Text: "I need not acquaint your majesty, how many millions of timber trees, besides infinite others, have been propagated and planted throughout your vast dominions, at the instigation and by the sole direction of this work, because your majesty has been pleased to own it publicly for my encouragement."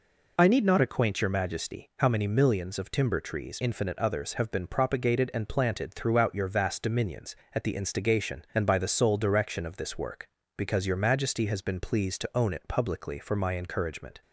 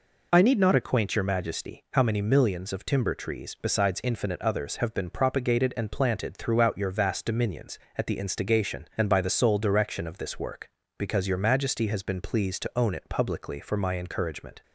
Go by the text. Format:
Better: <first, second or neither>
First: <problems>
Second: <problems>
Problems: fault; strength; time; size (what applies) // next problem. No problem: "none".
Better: second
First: skips "besides"; at 3.6 s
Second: none